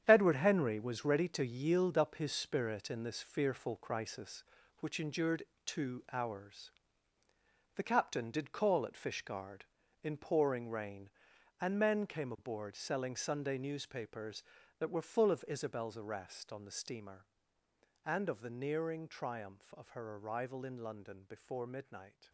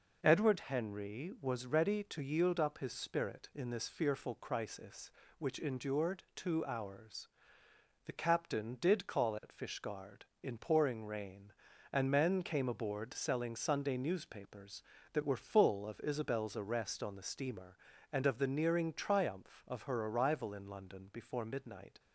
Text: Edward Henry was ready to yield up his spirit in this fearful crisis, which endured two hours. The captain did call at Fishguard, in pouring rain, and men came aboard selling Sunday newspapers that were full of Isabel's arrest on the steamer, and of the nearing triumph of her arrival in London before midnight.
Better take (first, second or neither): second